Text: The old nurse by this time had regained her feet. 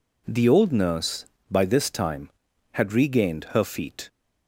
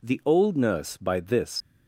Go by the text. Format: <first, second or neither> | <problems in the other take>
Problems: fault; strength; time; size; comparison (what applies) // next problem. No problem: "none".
first | stops before "time had regained her feet"; at 1.6 s